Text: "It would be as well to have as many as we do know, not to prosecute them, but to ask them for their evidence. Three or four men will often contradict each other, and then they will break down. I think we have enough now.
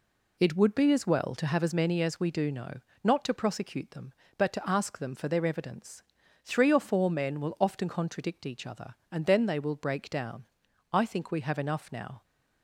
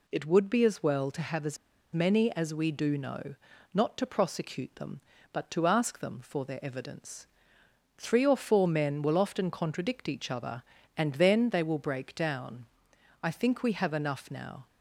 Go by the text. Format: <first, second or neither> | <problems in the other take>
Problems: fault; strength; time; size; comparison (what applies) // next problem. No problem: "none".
first | pauses between "as" and "many"; at 1.5 s; 0.37 s long